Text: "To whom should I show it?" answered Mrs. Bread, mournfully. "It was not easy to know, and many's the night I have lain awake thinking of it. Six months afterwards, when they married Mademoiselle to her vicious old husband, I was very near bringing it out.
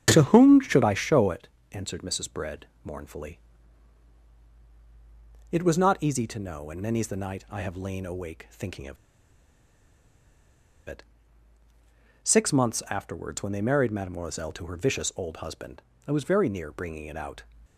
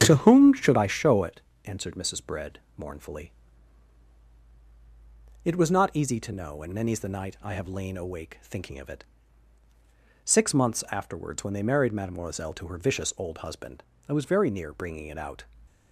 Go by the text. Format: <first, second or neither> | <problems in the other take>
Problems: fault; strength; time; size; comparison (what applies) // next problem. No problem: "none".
second | starts louder than the rest; strong; until 1.1 s; 8 dB; strong in the second // pauses between "of" and "it"; strong; at 8.9 s; 1.9 s long